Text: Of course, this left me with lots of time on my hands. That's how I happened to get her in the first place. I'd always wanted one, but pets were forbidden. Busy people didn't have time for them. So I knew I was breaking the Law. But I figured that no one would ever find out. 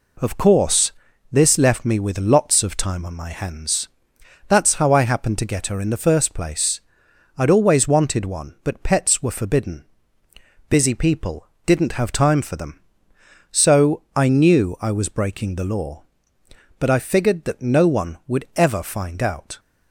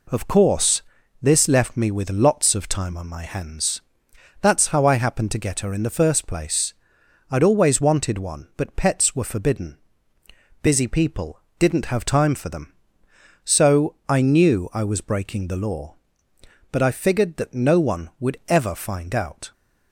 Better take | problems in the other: neither | pauses between "people" and "didn't"; slight; the same in both

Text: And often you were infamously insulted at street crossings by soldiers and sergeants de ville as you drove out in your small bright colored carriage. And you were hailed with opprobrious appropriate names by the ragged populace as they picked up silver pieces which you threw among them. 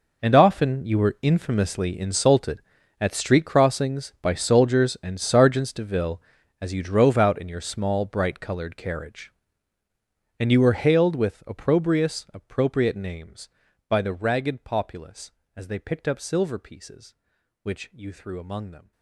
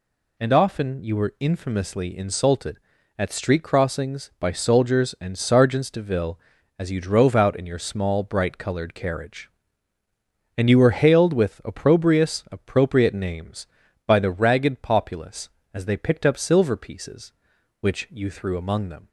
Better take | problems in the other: second | gets quieter; strong; throughout; 16.5 dB

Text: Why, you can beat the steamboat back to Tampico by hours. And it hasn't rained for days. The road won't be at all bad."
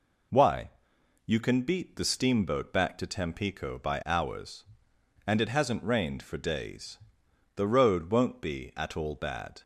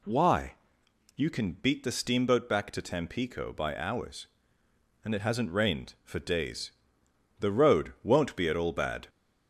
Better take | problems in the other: neither | none

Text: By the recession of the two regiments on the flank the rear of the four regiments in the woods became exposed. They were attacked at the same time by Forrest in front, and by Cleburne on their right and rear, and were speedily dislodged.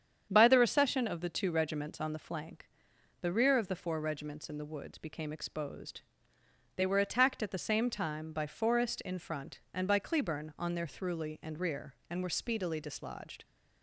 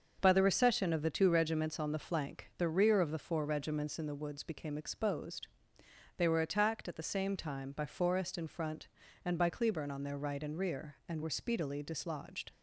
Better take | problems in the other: second | starts louder than the rest; strong; until 1.3 s; 8 dB; also in the second // pauses between "flank" and "the"; noticeable; at 2.6 s; 0.54 s long // says "thruly" for "right"; at 10.8 s

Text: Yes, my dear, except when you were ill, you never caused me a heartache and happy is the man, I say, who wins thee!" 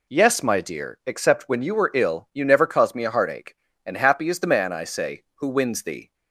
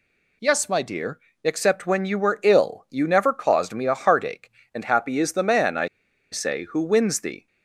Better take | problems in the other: first | pauses between "I" and "say"; at 5.8 s; 0.44 s long

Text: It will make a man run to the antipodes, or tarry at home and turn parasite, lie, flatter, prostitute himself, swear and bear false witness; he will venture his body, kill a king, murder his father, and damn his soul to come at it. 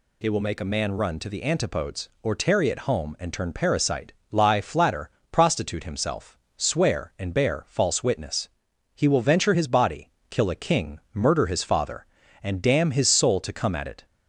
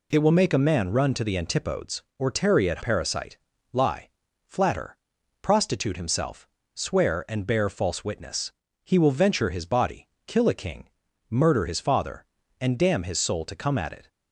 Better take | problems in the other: first | skips "home and turn"; at 2.8 s

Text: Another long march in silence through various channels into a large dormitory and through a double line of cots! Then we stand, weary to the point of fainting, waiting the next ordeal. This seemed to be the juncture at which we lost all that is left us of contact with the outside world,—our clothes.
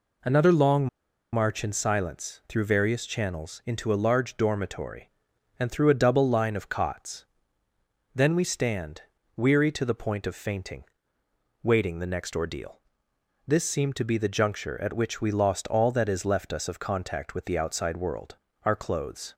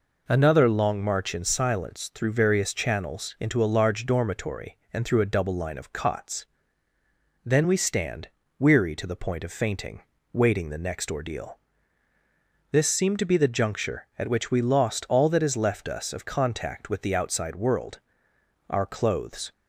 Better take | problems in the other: second | pauses between "long" and "march"; noticeable; at 0.8 s; 0.46 s long

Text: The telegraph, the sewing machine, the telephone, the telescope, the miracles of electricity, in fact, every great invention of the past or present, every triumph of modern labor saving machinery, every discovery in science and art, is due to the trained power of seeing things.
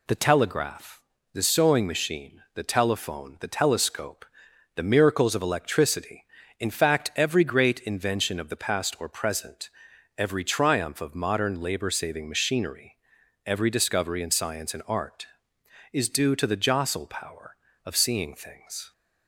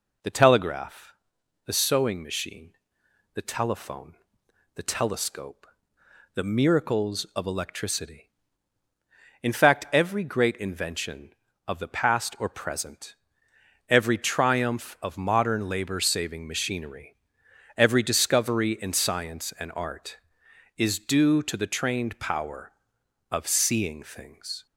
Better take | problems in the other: second | says "jostle" for "trained"; at 16.5 s

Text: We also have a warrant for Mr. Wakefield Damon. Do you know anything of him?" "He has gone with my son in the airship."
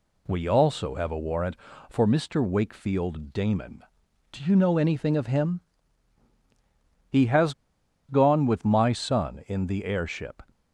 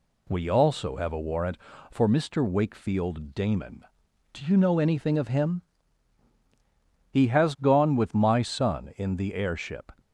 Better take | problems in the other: second | pauses between "has" and "gone"; noticeable; at 7.5 s; 0.56 s long

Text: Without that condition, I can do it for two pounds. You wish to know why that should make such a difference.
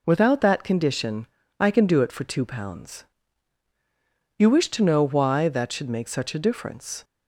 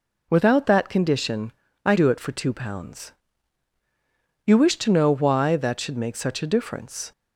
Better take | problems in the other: first | skips "can"; at 1.9 s

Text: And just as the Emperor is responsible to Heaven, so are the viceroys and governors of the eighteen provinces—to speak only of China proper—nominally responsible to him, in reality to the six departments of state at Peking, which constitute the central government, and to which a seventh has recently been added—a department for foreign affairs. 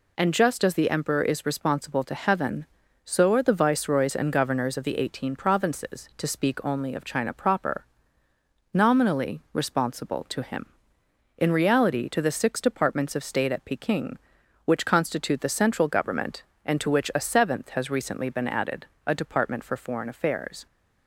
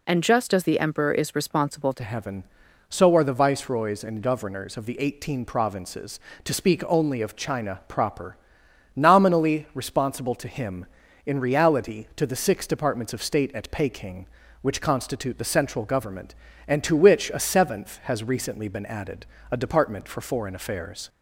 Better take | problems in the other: first | changes voice at "Heaven"; from 2.0 s on; 19.0 s long

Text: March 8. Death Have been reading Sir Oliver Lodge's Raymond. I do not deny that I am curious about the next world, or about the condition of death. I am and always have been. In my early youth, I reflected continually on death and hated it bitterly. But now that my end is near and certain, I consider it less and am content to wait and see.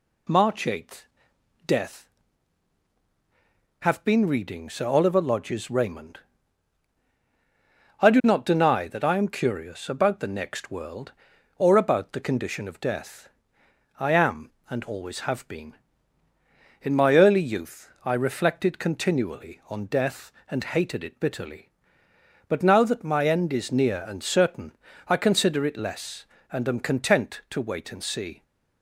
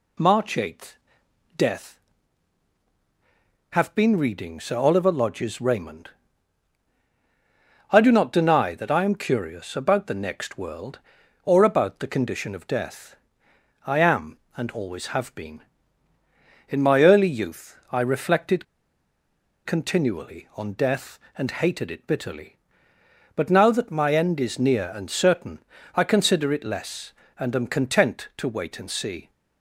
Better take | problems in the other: first | pauses between "reflected" and "continually"; at 18.6 s; 1.0 s long

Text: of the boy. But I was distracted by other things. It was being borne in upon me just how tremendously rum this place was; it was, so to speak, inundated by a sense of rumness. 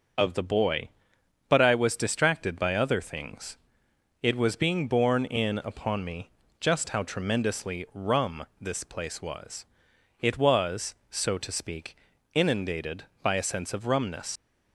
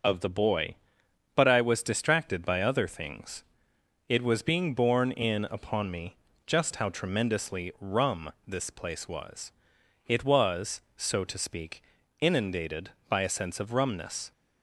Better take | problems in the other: second | pauses between "me" and "just"; slight; at 6.3 s; 0.28 s long; slight in the second // pauses between "rum" and "this"; slight; at 8.4 s; 0.16 s long; slight in the second // leaves "rumness" unfinished; at 14.3 s; 90 ms

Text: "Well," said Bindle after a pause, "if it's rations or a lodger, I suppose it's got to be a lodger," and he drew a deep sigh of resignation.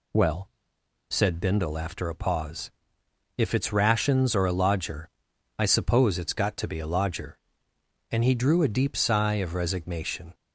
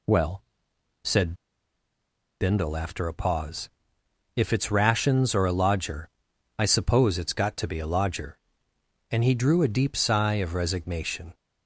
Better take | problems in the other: first | pauses between "said" and "Bindle"; at 1.3 s; 1.0 s long

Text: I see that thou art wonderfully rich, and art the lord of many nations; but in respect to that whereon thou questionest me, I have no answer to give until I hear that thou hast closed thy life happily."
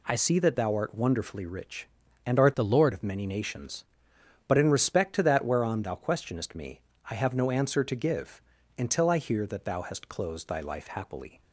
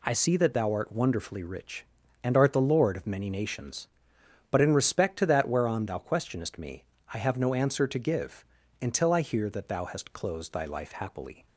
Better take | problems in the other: second | changes voice from "the" to "lord"; from 2.5 to 2.9 s; 0.4 s long // pauses between "give" and "until"; at 8.3 s; 0.38 s long; also in the second

